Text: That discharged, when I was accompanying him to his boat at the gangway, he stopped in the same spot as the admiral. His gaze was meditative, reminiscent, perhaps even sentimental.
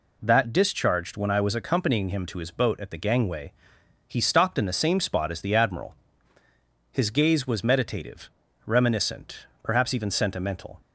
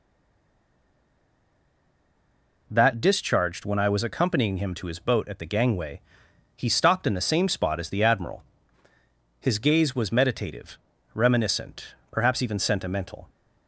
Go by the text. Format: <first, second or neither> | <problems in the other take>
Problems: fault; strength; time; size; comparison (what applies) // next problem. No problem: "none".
first | stays silent before the first word; strong; until 2.6 s; 2.6 s long